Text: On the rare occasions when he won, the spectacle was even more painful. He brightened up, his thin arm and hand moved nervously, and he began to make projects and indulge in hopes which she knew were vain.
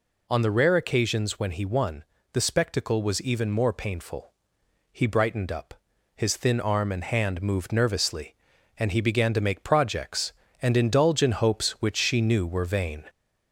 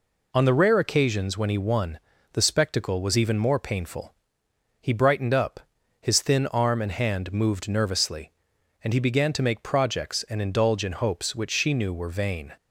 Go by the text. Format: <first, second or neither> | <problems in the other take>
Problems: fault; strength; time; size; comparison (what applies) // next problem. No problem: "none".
second | gets louder; slight; throughout; 2.5 dB